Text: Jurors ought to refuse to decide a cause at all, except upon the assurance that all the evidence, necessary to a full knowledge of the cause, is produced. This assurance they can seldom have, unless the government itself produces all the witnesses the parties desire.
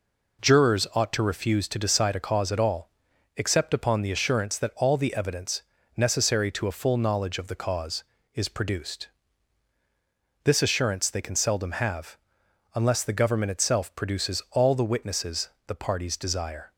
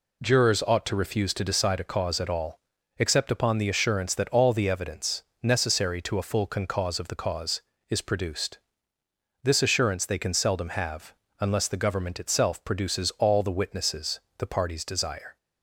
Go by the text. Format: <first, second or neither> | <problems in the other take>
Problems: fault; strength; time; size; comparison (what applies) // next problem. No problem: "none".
first | says "concause" for "knowledge"; at 6.4 s // pauses between "witnesses" and "the"; slight; at 14.1 s; 0.20 s long; slight in the first